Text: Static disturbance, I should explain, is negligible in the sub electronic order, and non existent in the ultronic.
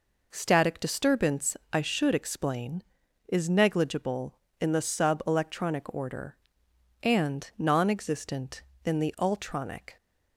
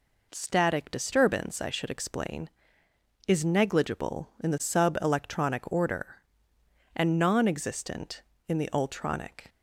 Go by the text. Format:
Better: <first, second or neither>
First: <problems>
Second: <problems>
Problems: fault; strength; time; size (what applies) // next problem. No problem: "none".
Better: neither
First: none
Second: none